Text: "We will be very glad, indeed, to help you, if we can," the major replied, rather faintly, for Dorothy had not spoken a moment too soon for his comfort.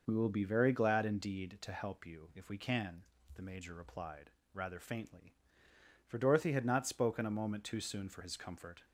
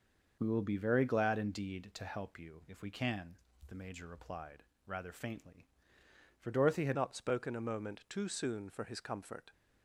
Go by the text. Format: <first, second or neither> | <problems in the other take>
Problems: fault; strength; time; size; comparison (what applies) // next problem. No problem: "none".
first | changes voice at "not"; from 6.9 s on; 2.6 s long